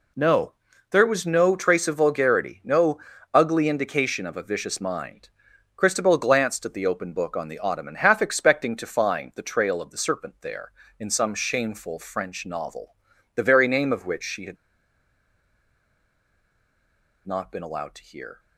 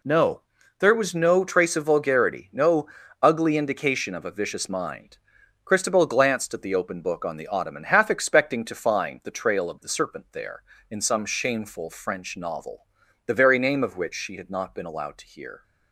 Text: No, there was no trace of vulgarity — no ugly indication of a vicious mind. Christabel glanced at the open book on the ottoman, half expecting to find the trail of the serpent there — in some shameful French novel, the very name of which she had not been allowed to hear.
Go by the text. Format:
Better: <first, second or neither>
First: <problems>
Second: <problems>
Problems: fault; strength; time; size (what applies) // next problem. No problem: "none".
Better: second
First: pauses between "no" and "ugly"; slight; at 2.9 s; 0.34 s long // pauses between "had" and "not"; strong; at 14.5 s; 2.7 s long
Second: pauses between "no" and "ugly"; slight; at 2.8 s; 0.34 s long